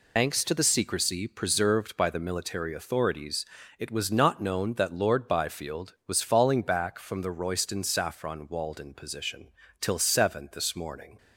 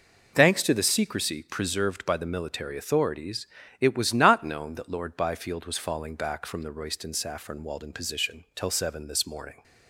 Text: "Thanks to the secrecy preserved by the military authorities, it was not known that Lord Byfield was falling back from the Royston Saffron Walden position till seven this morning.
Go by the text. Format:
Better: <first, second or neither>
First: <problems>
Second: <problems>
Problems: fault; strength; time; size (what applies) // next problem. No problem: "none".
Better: second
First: loses the start of "Thanks"; at 0.1 s; 65 ms // pauses between "position" and "till"; slight; at 9.5 s; 0.30 s long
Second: none